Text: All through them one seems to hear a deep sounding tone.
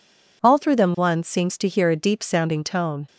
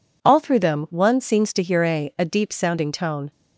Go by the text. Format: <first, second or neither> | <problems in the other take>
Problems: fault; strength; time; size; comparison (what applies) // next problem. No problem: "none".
first | says "a" twice; at 2.1 s